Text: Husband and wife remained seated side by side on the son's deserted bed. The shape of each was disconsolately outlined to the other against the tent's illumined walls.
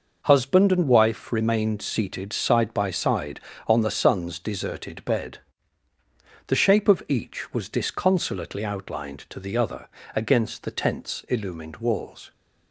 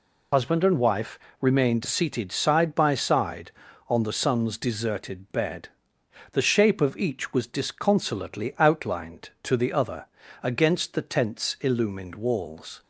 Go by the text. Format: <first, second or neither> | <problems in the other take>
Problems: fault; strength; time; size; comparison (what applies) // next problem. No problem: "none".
first | loses the start of "Husband"; at 0.3 s; 45 ms // pauses between "wife" and "remained"; slight; at 1.1 s; 0.20 s long // pauses between "other" and "against"; slight; at 10.0 s; 0.36 s long; slight in the first